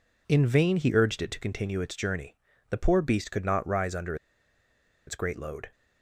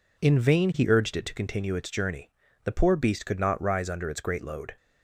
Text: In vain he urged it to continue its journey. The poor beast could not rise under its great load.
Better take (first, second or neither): second